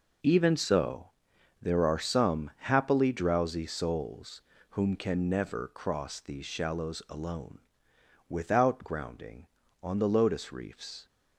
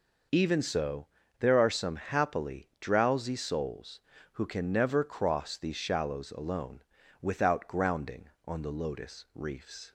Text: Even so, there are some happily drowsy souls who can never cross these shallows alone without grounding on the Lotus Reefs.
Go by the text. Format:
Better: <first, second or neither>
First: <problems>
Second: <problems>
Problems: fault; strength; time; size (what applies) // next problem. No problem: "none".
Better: second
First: says "whom" for "who"; at 4.6 s // pauses between "alone" and "without"; noticeable; at 7.5 s; 0.68 s long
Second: pauses between "alone" and "without"; at 6.8 s; 0.40 s long